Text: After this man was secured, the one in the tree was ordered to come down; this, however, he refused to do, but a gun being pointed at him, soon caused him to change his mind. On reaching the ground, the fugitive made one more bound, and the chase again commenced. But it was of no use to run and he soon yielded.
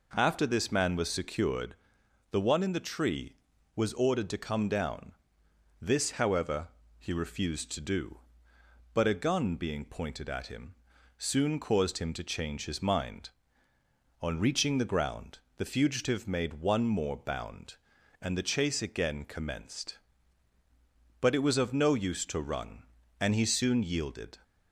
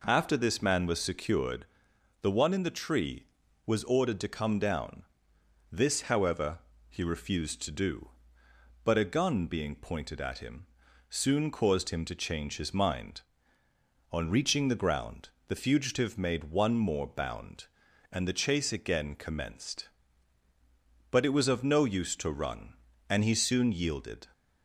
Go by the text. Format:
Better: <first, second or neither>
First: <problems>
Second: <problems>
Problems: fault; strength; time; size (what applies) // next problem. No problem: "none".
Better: neither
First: none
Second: none